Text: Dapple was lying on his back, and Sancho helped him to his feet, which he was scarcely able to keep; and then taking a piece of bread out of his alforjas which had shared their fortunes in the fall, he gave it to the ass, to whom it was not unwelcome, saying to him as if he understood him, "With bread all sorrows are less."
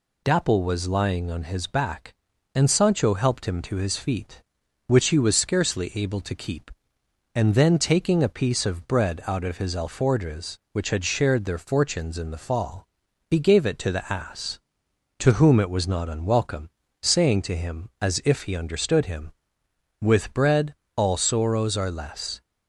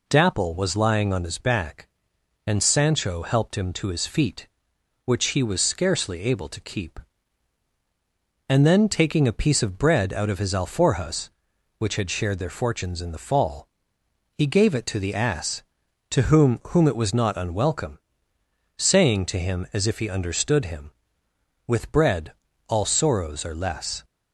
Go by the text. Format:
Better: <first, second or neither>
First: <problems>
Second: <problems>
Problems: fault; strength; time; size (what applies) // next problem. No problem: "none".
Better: first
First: pauses between "bread" and "all"; slight; at 20.7 s; 0.22 s long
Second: says "whom" twice; at 16.6 s // pauses between "bread" and "all"; slight; at 22.3 s; 0.36 s long